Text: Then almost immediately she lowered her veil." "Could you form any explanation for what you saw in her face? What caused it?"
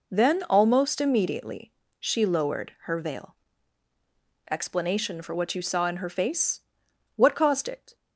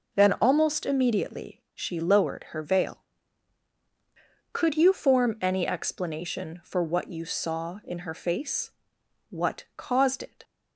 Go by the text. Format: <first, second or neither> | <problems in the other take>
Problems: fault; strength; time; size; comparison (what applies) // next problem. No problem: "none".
second | pauses between "immediately" and "she"; slight; at 1.7 s; 0.26 s long // skips "Could you form any"; at 3.9 s